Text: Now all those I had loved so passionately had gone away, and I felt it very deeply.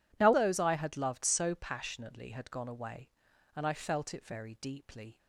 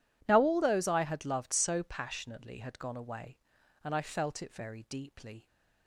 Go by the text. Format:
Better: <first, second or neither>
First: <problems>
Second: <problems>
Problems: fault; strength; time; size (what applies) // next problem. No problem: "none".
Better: second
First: skips "all"; at 0.3 s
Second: none